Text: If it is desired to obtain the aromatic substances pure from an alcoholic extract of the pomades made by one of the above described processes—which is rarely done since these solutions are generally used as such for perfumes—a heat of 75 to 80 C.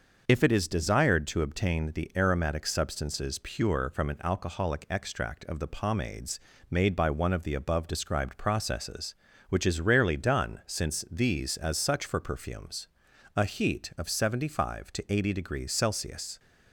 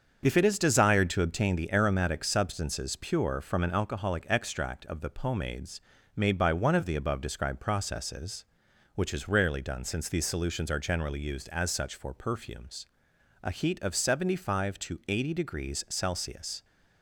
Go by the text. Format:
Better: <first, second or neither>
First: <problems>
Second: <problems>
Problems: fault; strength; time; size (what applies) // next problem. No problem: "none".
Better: second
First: starts louder than the rest; until 1.2 s; 6 dB // pauses between "pomades" and "made"; slight; at 6.3 s; 0.32 s long // skips "solutions are generally used"; at 11.5 s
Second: starts louder than the rest; until 1.2 s; 7 dB // pauses between "pomades" and "made"; slight; at 5.8 s; 0.34 s long